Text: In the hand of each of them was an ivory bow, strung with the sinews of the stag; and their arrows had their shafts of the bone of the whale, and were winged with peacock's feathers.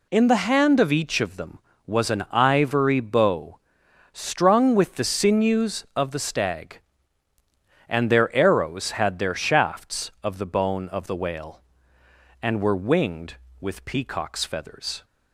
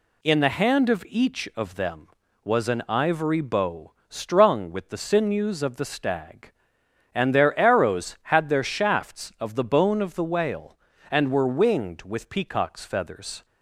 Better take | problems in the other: neither | none

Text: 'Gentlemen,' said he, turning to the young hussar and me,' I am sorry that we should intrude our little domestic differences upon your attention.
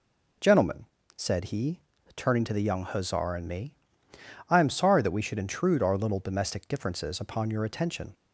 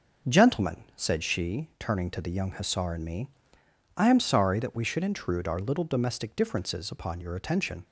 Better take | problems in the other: first | starts louder than the rest; noticeable; until 1.3 s; 6 dB // says "she" for "he"; at 1.2 s

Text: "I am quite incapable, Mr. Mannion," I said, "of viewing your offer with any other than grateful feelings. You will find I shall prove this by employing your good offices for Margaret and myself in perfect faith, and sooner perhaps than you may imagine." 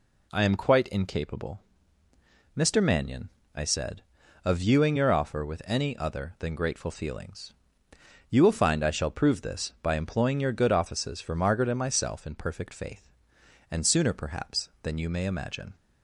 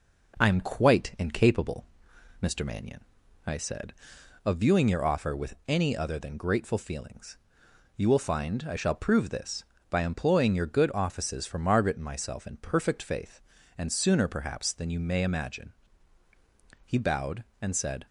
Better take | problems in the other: first | goes on to say "He bowed and said"; noticeable; from 16.8 s on; 1.2 s long

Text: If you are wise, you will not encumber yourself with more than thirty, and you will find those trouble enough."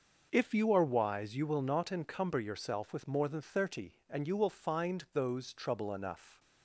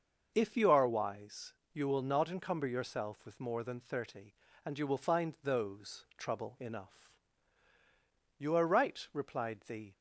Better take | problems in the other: first | starts louder than the rest; noticeable; until 1.3 s; 6 dB; noticeable in the first // goes on to say "You are right replied the"; from 8.3 s on; 1.5 s long

